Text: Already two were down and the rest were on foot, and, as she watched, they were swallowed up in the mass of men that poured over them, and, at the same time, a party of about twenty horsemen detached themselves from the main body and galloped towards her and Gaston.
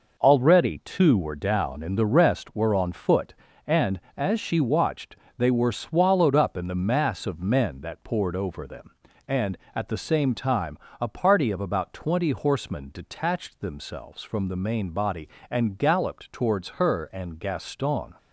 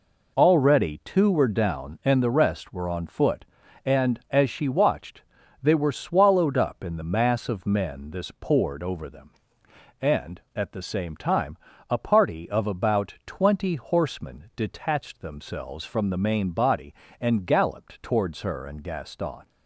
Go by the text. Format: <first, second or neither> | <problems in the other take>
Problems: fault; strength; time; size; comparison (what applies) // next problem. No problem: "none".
first | says "this" for "that"; at 8.1 s